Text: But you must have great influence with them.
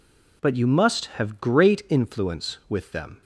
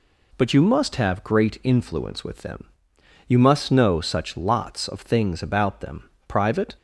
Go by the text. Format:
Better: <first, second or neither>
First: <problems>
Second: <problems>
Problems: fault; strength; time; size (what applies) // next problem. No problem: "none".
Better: first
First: none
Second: goes on to say "You must know such lots of things about them private"; strong; from 3.2 s on; 3.4 s long